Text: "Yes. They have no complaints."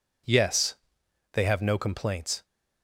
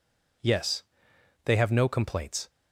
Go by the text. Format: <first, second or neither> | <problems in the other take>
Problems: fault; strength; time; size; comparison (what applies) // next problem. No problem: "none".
neither | none